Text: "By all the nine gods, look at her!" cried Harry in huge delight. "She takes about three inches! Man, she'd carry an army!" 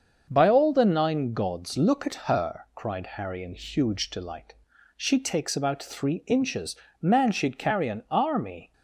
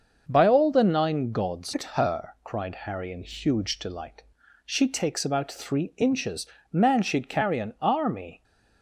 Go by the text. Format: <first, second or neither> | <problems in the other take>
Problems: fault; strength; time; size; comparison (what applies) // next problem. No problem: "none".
first | starts louder than the rest; until 1.2 s; 6.5 dB; also in the first // skips "look"; at 1.7 s